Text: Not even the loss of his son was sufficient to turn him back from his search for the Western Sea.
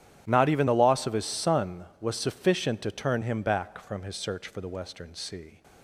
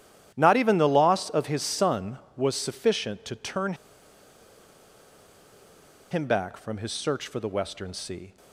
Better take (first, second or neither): first